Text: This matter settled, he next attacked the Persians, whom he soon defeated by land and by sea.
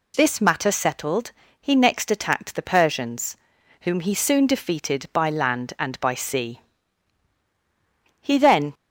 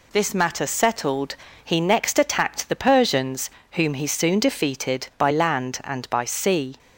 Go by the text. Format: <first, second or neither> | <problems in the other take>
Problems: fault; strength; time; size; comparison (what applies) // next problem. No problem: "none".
second | goes on to say "He then"; from 8.1 s on; 0.54 s long